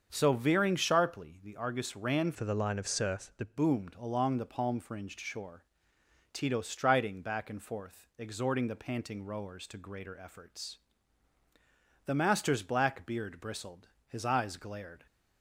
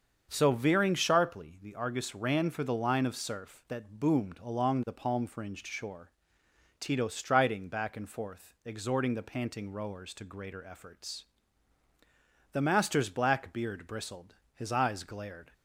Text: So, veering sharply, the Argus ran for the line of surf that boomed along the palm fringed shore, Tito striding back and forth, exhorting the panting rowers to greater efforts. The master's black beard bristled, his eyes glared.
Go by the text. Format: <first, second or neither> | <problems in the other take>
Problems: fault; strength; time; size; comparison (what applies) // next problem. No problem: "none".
second | starts louder than the rest; until 1.1 s; 7 dB; also in the second // changes voice from "for" to "that"; from 2.3 to 3.5 s; 1.2 s long